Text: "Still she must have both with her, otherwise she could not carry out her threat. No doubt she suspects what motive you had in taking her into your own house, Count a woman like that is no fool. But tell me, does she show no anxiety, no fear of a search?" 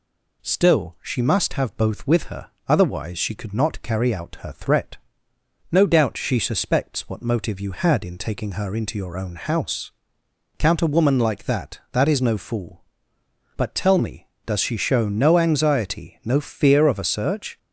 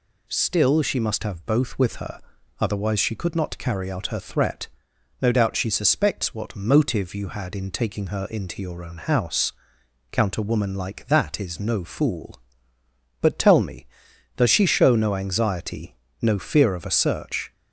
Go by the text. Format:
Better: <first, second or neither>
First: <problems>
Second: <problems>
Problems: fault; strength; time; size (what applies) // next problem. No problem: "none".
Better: second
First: says "that" twice; at 11.9 s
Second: none